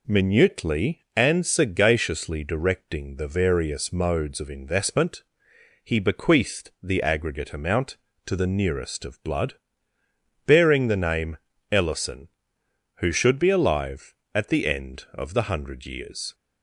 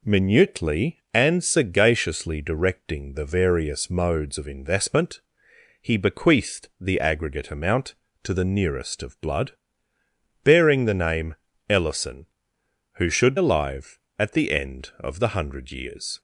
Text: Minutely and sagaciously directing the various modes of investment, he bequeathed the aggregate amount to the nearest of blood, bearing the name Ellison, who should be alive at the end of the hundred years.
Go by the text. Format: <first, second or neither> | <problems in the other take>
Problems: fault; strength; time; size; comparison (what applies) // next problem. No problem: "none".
first | pauses between "name" and "Ellison"; slight; at 11.3 s; 0.34 s long; slight in the first // skips "be"; at 13.3 s